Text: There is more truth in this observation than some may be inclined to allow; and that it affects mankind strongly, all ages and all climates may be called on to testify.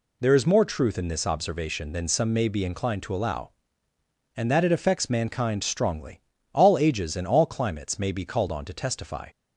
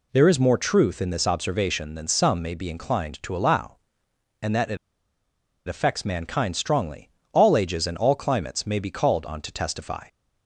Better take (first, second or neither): first